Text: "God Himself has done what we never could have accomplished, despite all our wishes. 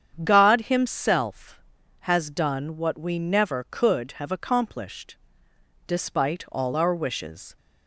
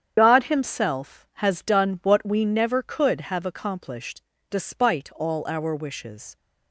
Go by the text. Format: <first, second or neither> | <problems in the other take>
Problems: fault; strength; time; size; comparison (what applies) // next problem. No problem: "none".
first | loses the start of "God"; at 0.1 s; 35 ms // starts louder than the rest; strong; until 1.1 s; 8.5 dB; strong in the first